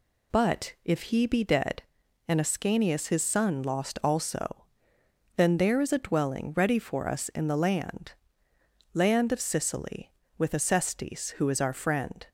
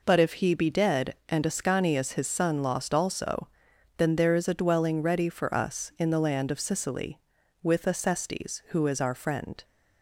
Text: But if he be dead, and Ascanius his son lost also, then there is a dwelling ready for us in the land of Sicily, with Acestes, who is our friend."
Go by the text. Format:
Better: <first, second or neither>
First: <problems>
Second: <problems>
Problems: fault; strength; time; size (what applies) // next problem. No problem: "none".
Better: second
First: says "land" twice; at 8.9 s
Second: none